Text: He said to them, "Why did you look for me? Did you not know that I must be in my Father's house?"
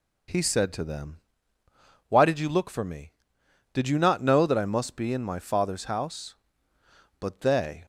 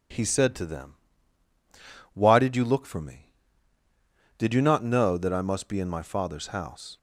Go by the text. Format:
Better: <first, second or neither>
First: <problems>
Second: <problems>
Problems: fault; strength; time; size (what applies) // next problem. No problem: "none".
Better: second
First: goes on to say "But they"; noticeable; from 7.1 s on; 0.66 s long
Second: none